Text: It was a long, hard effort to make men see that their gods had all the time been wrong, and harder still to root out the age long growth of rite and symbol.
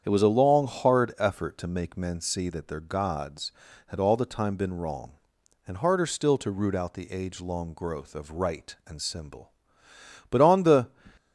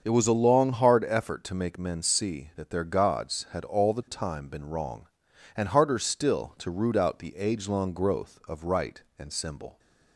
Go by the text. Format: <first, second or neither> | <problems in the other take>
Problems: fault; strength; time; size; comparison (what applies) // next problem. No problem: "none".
second | starts louder than the rest; strong; until 1.0 s; 8.5 dB; also in the second // goes on to say "But on the"; from 10.3 s on; 0.58 s long